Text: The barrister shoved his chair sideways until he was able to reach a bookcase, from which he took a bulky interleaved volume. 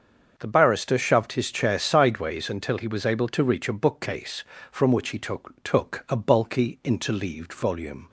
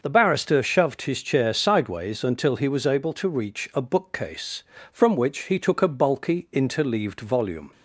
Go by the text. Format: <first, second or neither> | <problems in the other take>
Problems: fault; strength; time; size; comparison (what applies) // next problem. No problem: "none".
second | starts louder than the rest; until 1.3 s; 6.5 dB // says "took" twice; at 5.6 s